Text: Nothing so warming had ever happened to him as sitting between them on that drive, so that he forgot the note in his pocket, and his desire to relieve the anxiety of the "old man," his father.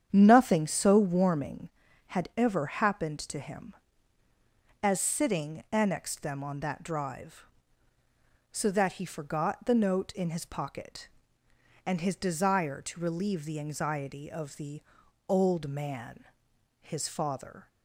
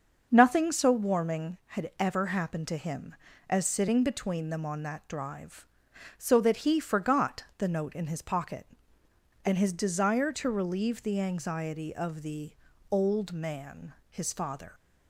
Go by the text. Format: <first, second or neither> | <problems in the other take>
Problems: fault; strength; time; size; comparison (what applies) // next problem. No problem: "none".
second | starts louder than the rest; strong; until 1.1 s; 8.5 dB; also in the second // says "annexed" for "between"; at 5.7 s // pauses between "the" and "old"; noticeable; at 14.8 s; 0.48 s long; also in the second